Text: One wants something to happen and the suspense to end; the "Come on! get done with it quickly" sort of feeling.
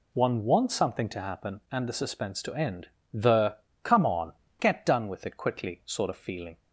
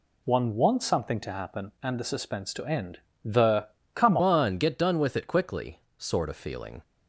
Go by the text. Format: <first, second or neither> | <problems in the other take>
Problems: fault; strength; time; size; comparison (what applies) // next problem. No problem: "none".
first | pauses between "the" and "Come"; slight; at 3.6 s; 0.26 s long; slight in the first // changes voice at "on"; from 4.2 s on; 2.6 s long // pauses between "quickly" and "sort"; slight; at 5.8 s; 0.18 s long